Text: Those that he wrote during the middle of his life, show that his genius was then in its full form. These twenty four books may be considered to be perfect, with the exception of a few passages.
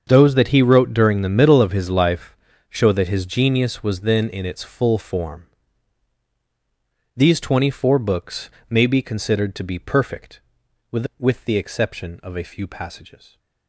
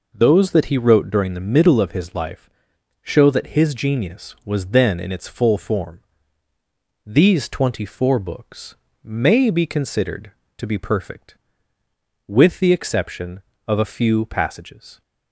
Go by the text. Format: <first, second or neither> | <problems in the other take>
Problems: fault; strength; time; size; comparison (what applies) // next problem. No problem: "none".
second | starts louder than the rest; until 1.0 s; 7 dB // pauses between "books" and "may"; slight; at 8.5 s; 0.20 s long; slight in the second // says "with" twice; at 11.1 s